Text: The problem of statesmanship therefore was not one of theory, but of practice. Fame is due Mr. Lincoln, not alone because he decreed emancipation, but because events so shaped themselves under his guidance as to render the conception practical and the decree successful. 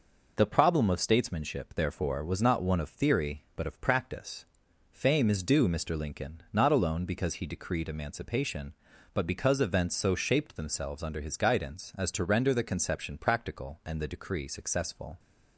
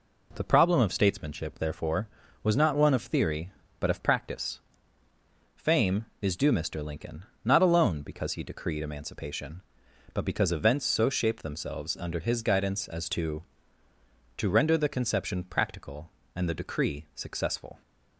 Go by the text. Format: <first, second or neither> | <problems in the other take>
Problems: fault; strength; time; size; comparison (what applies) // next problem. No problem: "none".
first | says "to" twice; at 14.3 s